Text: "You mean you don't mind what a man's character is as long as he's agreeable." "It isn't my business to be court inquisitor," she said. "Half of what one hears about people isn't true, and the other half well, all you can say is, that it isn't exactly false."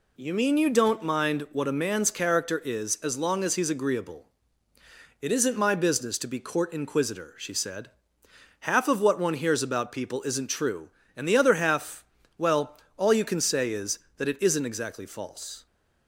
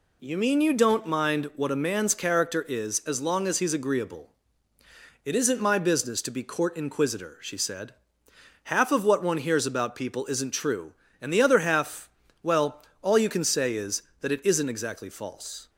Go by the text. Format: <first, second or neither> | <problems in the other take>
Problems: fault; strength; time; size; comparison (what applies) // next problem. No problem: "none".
neither | pauses between "half" and "well"; slight; the same in both